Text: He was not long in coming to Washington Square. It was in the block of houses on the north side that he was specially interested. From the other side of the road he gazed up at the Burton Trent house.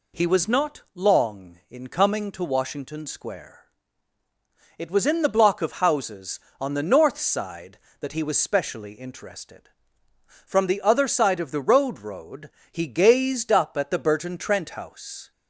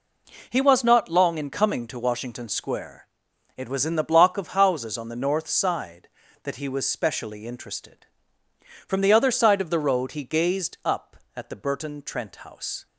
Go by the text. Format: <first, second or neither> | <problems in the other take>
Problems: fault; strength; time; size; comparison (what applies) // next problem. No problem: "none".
second | says "road" twice; at 11.9 s